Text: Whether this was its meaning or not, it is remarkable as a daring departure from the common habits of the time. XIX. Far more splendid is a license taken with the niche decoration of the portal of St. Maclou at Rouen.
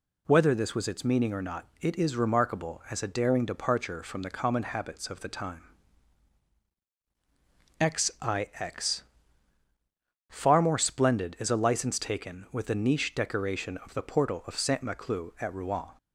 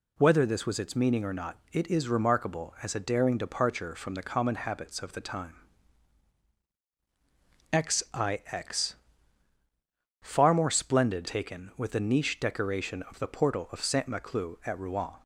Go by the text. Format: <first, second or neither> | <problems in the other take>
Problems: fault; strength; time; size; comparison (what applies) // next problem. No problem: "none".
first | skips "is a license"; at 11.2 s